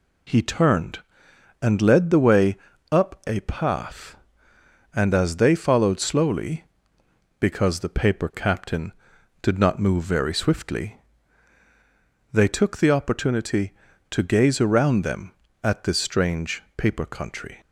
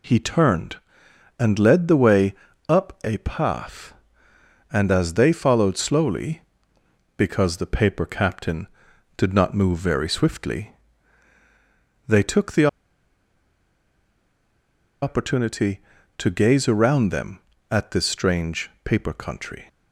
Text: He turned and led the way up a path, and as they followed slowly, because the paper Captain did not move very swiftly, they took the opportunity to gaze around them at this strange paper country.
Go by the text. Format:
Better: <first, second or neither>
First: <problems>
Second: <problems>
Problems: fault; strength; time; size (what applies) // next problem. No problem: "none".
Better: first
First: pauses between "way" and "up"; slight; at 2.5 s; 0.34 s long // pauses between "a" and "path"; slight; at 3.3 s; 0.20 s long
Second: pauses between "way" and "up"; slight; at 2.3 s; 0.34 s long // pauses between "a" and "path"; slight; at 3.1 s; 0.20 s long // pauses between "the" and "opportunity"; strong; at 12.6 s; 2.3 s long